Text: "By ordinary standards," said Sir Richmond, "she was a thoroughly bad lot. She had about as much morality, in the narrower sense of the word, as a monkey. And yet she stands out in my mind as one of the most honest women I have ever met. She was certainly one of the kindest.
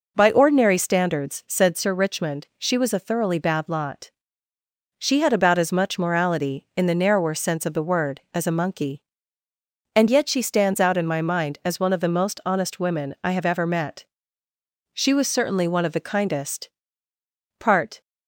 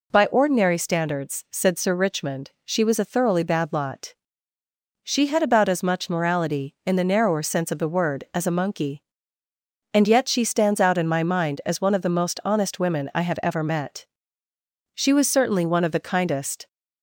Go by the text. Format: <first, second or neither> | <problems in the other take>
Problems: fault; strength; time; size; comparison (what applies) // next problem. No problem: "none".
second | goes on to say "Part"; slight; from 17.6 s on; 0.40 s long